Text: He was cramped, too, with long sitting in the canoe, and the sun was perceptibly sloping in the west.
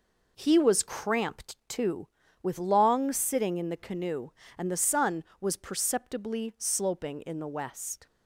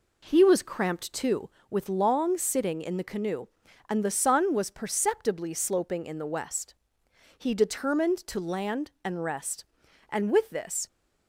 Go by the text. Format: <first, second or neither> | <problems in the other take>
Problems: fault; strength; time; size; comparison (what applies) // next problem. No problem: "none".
first | goes on to say "He determined to land and rest and with this"; strong; from 7.3 s on; 3.5 s long